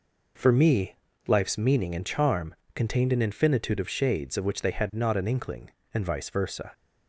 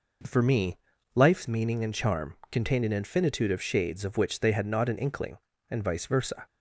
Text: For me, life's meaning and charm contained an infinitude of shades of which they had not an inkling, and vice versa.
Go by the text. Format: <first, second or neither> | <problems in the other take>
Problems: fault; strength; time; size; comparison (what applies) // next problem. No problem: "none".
neither | pauses between "charm" and "contained"; slight; the same in both